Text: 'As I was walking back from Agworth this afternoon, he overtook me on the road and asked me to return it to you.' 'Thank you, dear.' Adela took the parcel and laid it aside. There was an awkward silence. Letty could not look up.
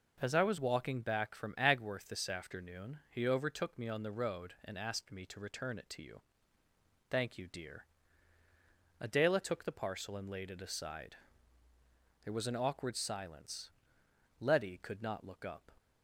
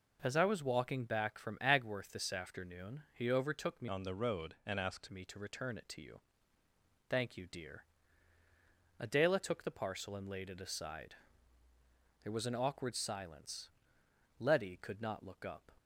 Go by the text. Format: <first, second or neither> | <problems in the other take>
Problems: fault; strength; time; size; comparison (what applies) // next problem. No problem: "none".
first | changes voice from "on" to "asked"; from 3.8 to 5.0 s; 1.2 s long